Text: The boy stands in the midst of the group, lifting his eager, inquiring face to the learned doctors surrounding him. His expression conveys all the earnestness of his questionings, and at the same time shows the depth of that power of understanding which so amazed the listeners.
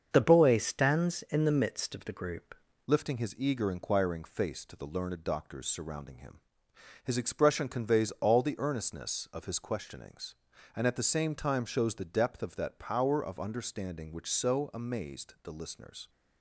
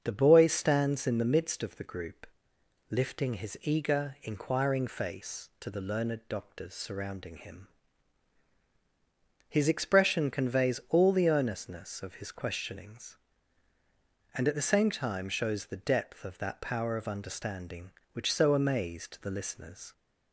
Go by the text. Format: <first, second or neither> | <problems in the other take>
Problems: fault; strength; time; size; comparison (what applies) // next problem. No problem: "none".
second | starts louder than the rest; until 1.1 s; 7 dB; also in the second // changes voice at "lifting"; from 2.8 s on; 13.2 s long